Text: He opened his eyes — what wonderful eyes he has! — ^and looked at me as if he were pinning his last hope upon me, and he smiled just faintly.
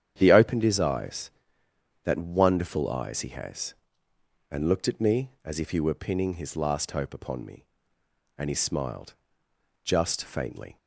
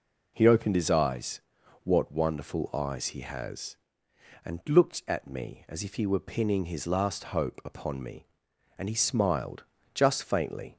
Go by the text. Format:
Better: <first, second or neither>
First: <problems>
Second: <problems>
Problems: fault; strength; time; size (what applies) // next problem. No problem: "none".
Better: second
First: starts louder than the rest; strong; until 1.1 s; 9 dB // says "that" for "what"; at 2.0 s // pauses between "smiled" and "just"; noticeable; at 9.1 s; 0.72 s long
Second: pauses between "smiled" and "just"; slight; at 9.6 s; 0.32 s long